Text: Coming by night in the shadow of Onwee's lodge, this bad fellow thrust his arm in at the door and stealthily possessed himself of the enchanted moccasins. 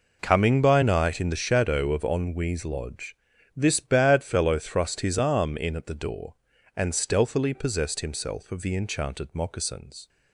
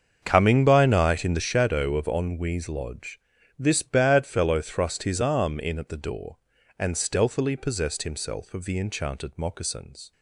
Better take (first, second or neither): first